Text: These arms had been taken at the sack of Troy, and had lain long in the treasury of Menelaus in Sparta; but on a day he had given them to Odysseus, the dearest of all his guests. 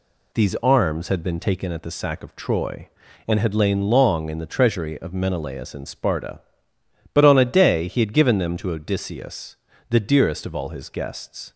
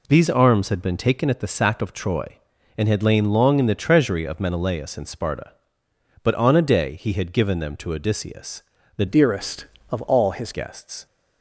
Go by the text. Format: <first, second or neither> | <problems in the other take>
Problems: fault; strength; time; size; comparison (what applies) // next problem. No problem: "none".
first | changes voice from "dearest" to "his"; from 9.0 to 10.5 s; 1.5 s long